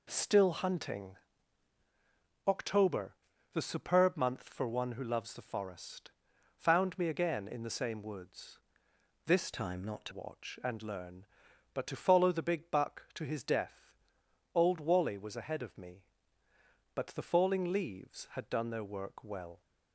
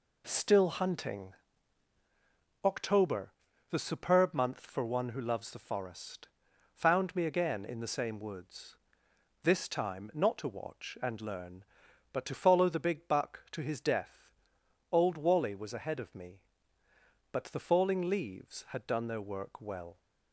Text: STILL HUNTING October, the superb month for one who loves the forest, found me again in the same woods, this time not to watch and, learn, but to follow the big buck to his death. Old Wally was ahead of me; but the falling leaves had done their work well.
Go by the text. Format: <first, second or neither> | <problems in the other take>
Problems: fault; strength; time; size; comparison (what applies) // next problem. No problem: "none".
second | pauses between "HUNTING" and "October"; strong; at 1.1 s; 1.3 s long; strong in the second // changes voice from "time" to "to"; from 9.5 to 10.1 s; 0.6 s long